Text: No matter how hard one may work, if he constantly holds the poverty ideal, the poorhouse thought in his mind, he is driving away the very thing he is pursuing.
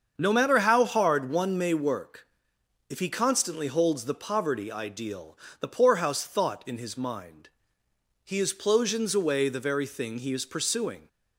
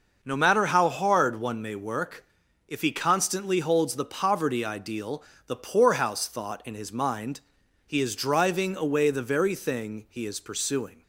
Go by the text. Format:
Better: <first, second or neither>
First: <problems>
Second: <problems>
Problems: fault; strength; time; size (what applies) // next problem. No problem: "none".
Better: second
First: starts louder than the rest; until 1.1 s; 7 dB // says "plosions" for "driving"; at 8.5 s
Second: none